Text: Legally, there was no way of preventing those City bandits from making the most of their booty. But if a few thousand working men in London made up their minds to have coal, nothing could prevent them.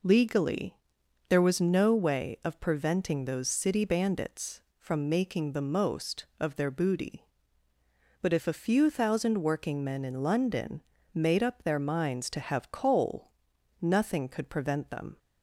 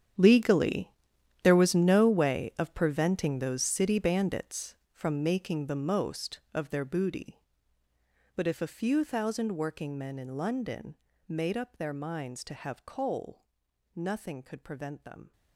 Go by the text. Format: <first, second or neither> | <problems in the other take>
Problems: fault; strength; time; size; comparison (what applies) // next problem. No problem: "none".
first | gets quieter; strong; throughout; 16.5 dB // pauses between "London" and "made"; slight; at 10.9 s; 0.32 s long; slight in the first